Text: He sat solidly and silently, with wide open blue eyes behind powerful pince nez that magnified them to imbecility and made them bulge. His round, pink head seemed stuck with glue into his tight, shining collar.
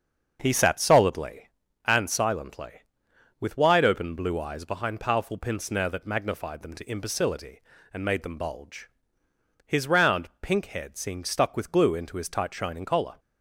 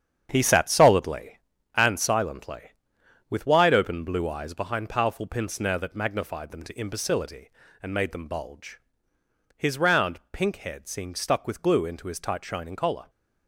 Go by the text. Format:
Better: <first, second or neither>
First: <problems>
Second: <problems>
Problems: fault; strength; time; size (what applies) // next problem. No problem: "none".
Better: first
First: starts louder than the rest; until 1.4 s; 6.5 dB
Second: gets quieter; strong; throughout; 8.5 dB // starts louder than the rest; strong; until 1.3 s; 8.5 dB